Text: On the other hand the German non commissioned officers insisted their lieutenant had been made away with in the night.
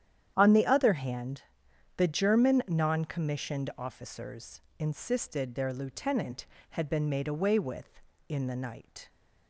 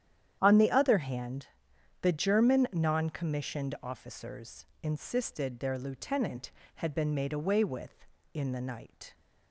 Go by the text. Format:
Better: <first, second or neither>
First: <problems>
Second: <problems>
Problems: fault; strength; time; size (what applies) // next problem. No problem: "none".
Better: neither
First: starts louder than the rest; strong; until 1.3 s; 10 dB // pauses between "hand" and "the"; noticeable; at 1.4 s; 0.54 s long // pauses between "officers" and "insisted"; slight; at 4.6 s; 0.20 s long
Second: starts louder than the rest; strong; until 1.4 s; 10 dB // pauses between "hand" and "the"; noticeable; at 1.4 s; 0.54 s long // pauses between "officers" and "insisted"; slight; at 4.6 s; 0.18 s long